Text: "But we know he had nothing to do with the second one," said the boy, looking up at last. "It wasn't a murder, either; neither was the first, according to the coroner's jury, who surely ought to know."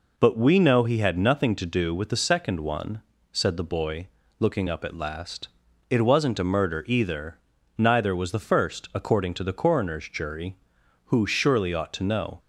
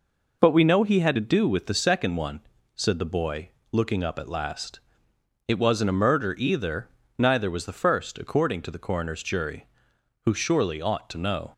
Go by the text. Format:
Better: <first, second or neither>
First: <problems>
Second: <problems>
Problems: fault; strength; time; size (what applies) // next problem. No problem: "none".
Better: first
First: none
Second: skips "nothing"; at 1.1 s